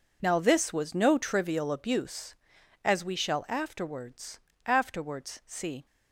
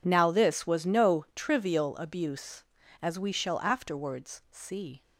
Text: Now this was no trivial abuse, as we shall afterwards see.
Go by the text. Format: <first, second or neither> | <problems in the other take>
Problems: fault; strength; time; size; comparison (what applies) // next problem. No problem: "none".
second | says "afterwards" twice; at 4.6 s